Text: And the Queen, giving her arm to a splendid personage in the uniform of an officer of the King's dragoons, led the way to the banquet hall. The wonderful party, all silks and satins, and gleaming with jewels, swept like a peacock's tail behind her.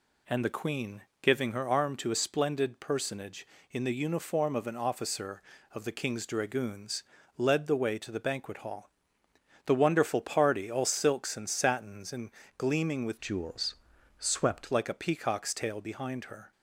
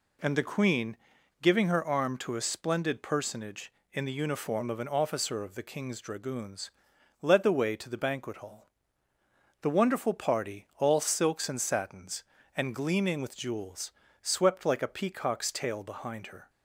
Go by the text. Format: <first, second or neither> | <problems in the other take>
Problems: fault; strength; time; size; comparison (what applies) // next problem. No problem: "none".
second | pauses between "and" and "gleaming"; slight; at 12.2 s; 0.28 s long // changes voice from "jewels" to "swept"; from 13.2 to 14.7 s; 1.5 s long